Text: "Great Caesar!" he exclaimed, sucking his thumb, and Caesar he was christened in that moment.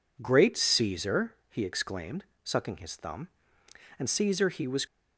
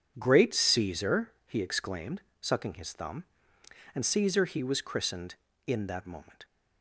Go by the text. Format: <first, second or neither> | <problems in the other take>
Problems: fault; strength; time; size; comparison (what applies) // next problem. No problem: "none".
second | stops before "christened in that moment"; at 4.8 s